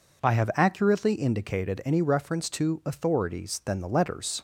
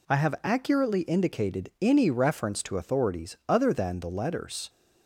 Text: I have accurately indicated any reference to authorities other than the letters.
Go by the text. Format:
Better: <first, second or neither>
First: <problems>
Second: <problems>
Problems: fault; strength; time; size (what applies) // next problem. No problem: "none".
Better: second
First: skips "other"; at 3.6 s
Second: none